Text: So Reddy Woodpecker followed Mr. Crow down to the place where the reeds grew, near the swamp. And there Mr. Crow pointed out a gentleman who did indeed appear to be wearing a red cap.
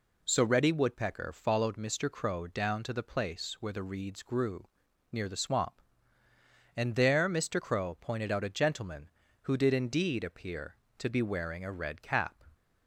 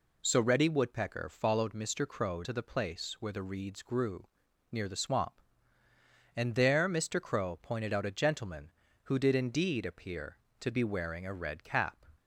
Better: first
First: none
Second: skips "down"; at 2.4 s

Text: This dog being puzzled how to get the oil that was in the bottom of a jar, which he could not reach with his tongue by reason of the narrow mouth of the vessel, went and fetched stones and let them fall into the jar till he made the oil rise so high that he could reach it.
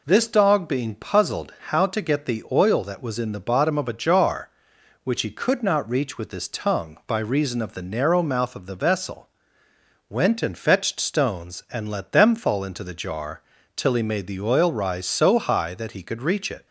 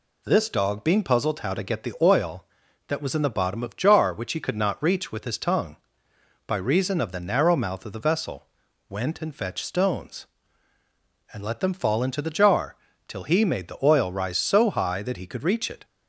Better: first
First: pauses between "jar" and "till"; slight; at 13.4 s; 0.36 s long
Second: skips "a"; at 3.7 s // pauses between "jar" and "till"; slight; at 12.7 s; 0.32 s long

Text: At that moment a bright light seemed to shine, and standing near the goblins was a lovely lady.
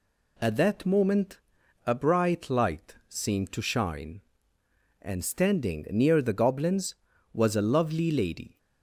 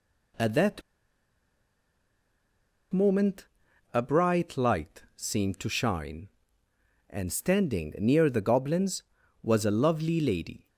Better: first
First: pauses between "moment" and "a"; noticeable; at 1.3 s; 0.46 s long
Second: pauses between "that" and "moment"; strong; at 0.8 s; 2.1 s long // pauses between "moment" and "a"; noticeable; at 3.4 s; 0.46 s long

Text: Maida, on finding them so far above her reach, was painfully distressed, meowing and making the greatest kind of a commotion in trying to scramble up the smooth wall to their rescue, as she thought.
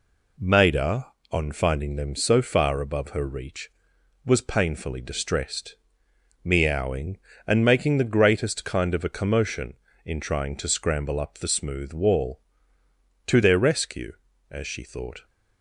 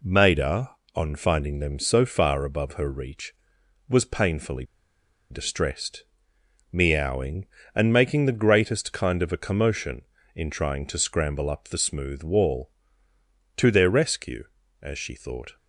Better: first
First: none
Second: pauses between "painfully" and "distressed"; noticeable; at 4.6 s; 0.66 s long

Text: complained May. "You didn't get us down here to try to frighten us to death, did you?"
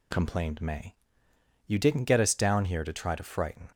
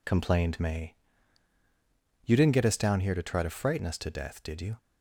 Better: second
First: stops before "us to death did you"; at 3.7 s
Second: none

